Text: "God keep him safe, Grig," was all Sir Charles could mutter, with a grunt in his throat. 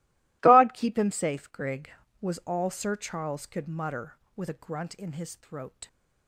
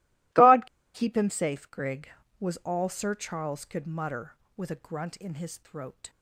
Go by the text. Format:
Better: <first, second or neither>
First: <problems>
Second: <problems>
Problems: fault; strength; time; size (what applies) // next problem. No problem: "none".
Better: first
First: none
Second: pauses between "God" and "keep"; slight; at 0.6 s; 0.28 s long